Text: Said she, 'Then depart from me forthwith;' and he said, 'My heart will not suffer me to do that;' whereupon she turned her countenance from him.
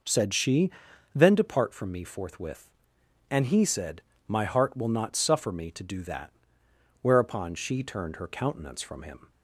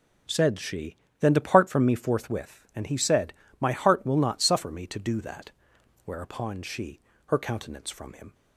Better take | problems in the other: first | skips "turned"; at 7.1 s

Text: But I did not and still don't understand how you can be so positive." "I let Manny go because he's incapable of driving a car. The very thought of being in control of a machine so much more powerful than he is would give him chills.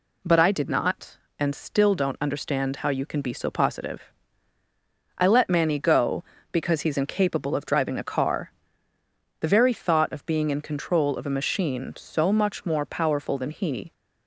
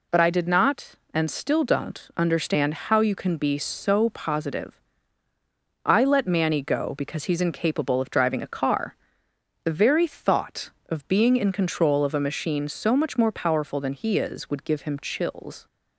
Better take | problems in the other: second | stops before "is would give him chills"; at 13.9 s

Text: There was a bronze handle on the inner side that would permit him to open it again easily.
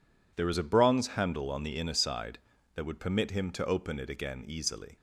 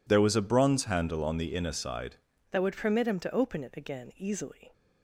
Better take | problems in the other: first | changes voice at "that"; from 2.5 s on; 2.2 s long

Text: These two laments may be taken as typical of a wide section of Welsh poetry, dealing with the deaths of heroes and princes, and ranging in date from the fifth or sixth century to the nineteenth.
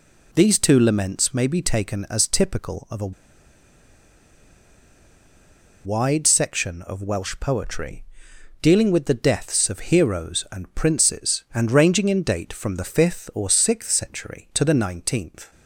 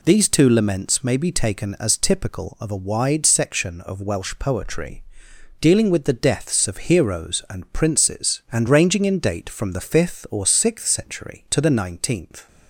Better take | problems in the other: second | pauses between "a" and "wide"; strong; at 3.1 s; 2.7 s long

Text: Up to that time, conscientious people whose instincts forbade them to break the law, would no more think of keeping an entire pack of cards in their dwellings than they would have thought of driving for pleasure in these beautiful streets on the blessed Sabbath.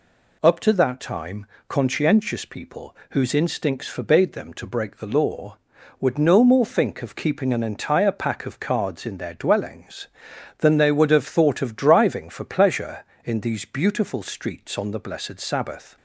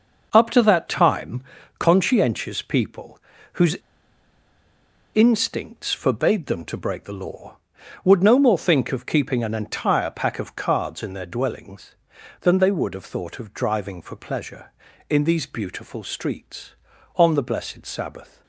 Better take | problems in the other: first | pauses between "people" and "whose"; slight; at 3.1 s; 0.36 s long; slight in the first // pauses between "whose" and "instincts"; strong; at 3.7 s; 1.3 s long

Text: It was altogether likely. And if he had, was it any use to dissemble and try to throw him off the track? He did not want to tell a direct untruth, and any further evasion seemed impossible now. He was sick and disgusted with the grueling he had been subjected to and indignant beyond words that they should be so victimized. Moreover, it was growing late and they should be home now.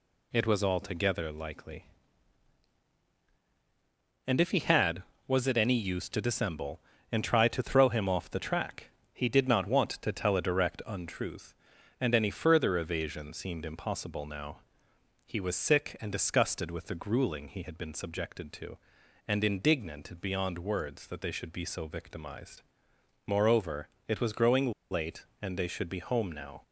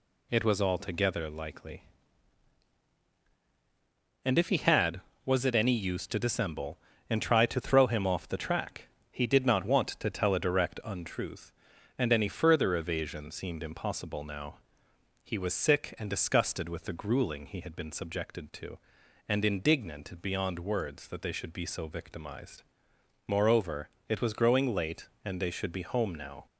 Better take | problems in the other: second | pauses between "growing" and "late"; slight; at 24.7 s; 0.18 s long

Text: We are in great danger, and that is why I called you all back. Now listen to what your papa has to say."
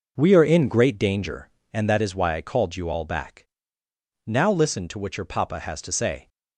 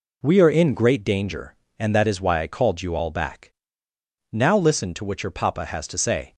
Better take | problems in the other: second | starts louder than the rest; noticeable; until 1.9 s; 5.5 dB

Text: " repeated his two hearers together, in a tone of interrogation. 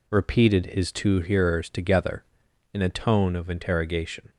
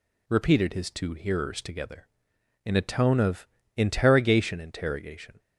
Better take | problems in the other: first | pauses between "of" and "interrogation"; slight; at 3.4 s; 0.30 s long // says "interrogation" twice; at 4.5 s

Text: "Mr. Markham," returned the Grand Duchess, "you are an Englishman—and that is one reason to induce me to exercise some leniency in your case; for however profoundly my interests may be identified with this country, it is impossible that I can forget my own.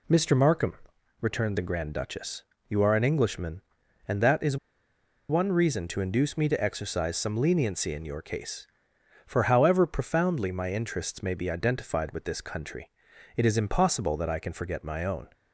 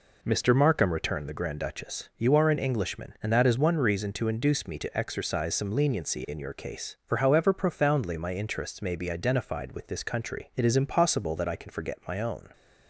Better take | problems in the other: second | pauses between "is" and "one"; noticeable; at 4.5 s; 0.73 s long

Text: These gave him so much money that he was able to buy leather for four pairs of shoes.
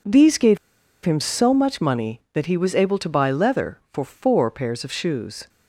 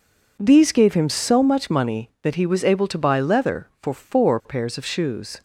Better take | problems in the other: second | pauses between "gave" and "him"; at 0.5 s; 0.45 s long

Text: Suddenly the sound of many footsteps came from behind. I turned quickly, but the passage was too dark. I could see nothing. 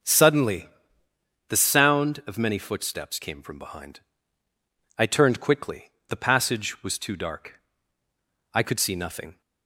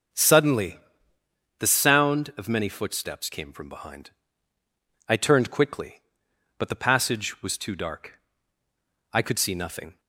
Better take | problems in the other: second | starts louder than the rest; until 1.8 s; 6.5 dB; also in the second // pauses between "Suddenly" and "the"; noticeable; at 0.6 s; 0.82 s long; noticeable in the second // skips "but"; at 5.9 s

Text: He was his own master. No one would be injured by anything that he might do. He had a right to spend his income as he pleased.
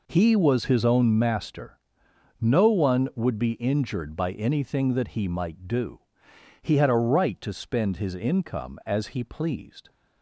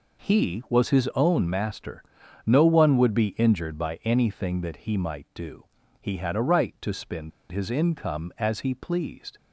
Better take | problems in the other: first | pauses between "spend" and "his"; slight; at 7.3 s; 0.20 s long

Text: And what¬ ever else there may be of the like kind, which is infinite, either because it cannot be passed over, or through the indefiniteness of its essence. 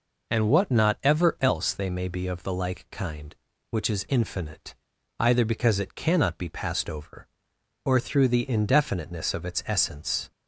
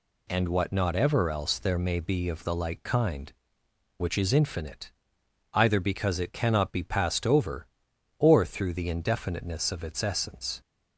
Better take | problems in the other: second | says "they" for "there"; at 1.7 s

